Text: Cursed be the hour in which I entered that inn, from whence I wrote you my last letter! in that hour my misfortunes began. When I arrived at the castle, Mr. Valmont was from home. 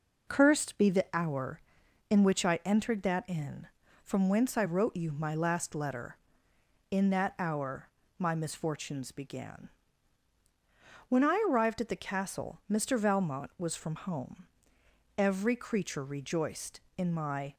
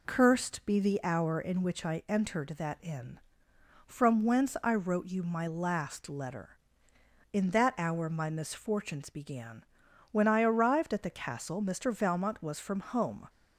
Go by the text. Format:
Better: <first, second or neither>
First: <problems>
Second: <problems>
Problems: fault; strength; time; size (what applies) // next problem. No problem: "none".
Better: second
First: pauses between "hour" and "my"; slight; at 7.8 s; 0.32 s long // goes on to say "Every creature rejoiced in my"; strong; from 15.1 s on; 2.3 s long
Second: none